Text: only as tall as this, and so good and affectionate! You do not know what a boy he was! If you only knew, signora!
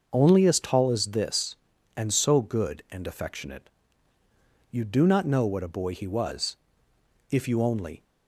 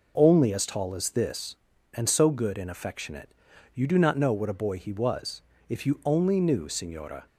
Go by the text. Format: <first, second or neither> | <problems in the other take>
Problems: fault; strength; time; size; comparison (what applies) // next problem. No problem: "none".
second | starts louder than the rest; noticeable; until 1.1 s; 6 dB // stops before "knew signora"; at 8.0 s